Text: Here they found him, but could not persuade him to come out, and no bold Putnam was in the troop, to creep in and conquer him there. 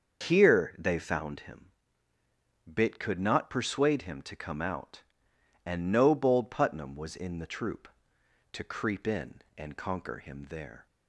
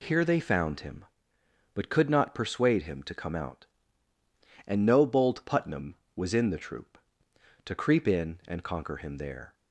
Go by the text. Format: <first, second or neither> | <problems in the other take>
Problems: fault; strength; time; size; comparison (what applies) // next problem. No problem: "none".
second | starts louder than the rest; until 1.3 s; 6.5 dB // says "bit" for "but"; at 2.7 s